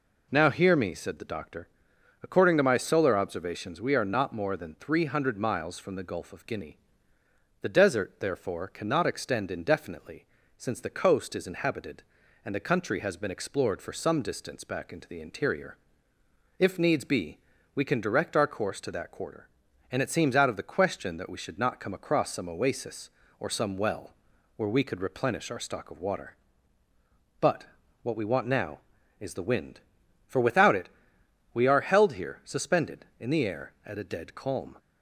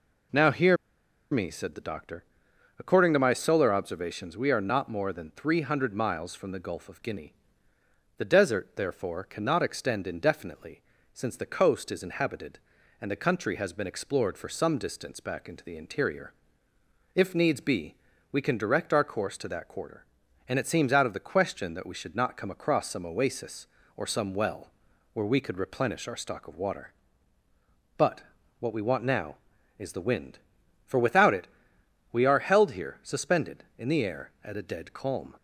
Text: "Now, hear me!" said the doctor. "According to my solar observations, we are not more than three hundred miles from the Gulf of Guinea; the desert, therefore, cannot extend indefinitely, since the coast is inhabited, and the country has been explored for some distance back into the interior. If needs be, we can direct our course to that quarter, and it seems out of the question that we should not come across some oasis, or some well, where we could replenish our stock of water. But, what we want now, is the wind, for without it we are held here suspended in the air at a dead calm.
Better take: first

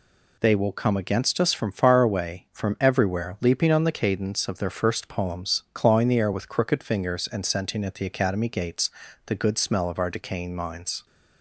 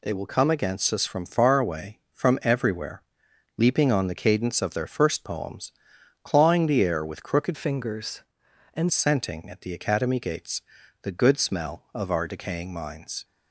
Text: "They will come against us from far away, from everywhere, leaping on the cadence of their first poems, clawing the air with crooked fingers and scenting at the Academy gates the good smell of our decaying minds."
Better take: first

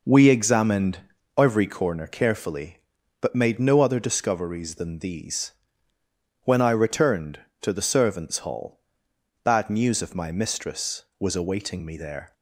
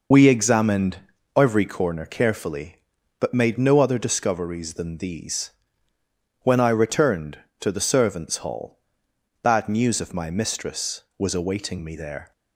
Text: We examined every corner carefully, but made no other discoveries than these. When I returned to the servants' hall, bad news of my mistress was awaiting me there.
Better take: first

